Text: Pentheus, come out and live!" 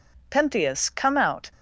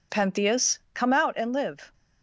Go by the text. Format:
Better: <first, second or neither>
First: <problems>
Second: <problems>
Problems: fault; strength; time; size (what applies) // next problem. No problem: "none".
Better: second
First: stops before "and live"; at 1.5 s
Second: none